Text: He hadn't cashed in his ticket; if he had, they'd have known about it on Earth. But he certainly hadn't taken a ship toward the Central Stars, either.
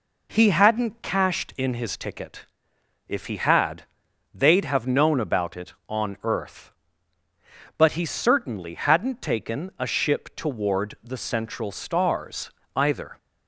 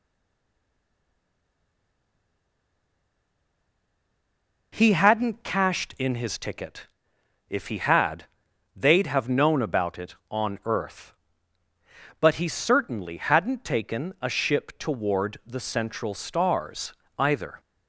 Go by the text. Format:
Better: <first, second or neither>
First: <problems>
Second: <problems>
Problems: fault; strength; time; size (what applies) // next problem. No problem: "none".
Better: first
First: none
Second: stays silent before the first word; strong; until 4.7 s; 4.7 s long